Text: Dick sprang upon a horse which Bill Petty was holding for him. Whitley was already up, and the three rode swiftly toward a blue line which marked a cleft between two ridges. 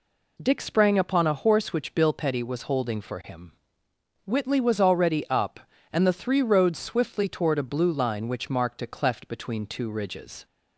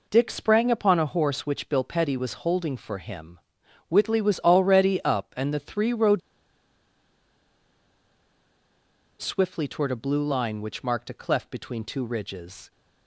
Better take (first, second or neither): first